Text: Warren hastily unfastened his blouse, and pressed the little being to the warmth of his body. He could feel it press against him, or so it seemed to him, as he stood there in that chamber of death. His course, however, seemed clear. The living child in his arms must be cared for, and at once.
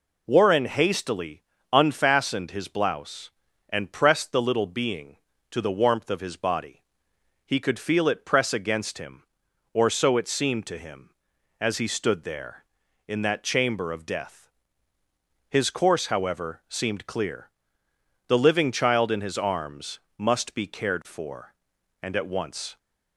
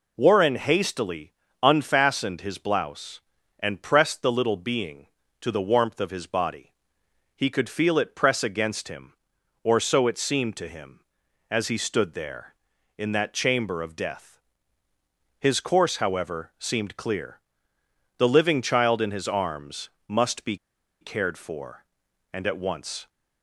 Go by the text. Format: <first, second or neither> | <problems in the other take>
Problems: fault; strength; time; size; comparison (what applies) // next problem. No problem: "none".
first | pauses between "hastily" and "unfastened"; slight; at 1.3 s; 0.28 s long; slight in the first // pauses between "arms" and "must"; slight; at 19.8 s; 0.18 s long; slight in the first // pauses between "be" and "cared"; at 20.5 s; 0.45 s long